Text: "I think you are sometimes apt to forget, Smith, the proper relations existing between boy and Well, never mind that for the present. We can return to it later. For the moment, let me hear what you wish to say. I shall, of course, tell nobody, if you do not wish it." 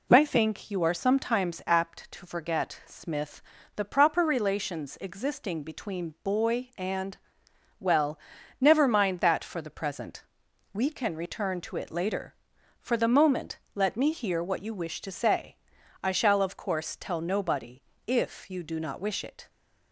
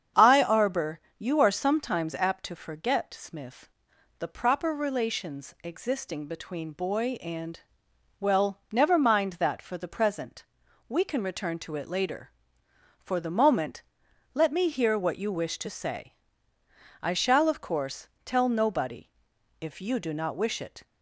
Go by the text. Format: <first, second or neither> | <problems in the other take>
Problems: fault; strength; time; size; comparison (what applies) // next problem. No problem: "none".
first | starts louder than the rest; strong; until 1.3 s; 7.5 dB // says "arbor" for "think"; at 0.4 s // pauses between "and" and "Well"; noticeable; at 7.5 s; 0.62 s long; noticeable in the first